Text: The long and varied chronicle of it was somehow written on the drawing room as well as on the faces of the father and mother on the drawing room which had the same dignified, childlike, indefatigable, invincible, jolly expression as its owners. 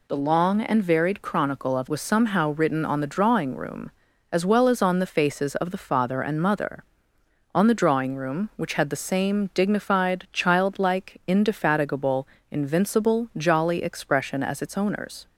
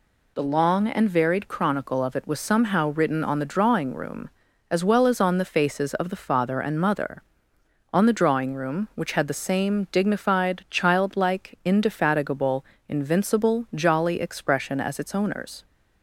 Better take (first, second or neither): second